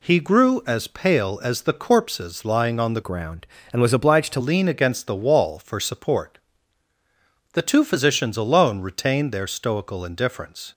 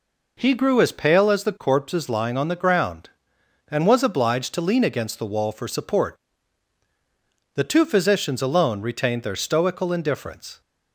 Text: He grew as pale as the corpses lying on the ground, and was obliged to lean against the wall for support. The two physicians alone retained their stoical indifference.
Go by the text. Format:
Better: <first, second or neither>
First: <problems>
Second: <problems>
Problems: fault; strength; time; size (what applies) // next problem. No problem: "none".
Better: second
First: changes voice from "ground" to "to"; from 3.0 to 4.4 s; 1.4 s long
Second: none